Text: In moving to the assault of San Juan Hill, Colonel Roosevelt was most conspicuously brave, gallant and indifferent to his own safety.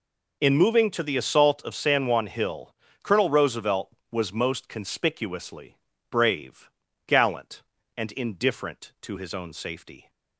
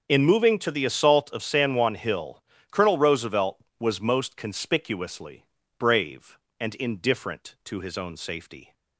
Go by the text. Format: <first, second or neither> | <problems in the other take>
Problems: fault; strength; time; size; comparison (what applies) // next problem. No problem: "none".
first | starts louder than the rest; until 1.1 s; 7 dB // pauses between "conspicuously" and "brave"; slight; at 5.4 s; 0.34 s long; slight in the first // skips "gallant"; at 6.4 s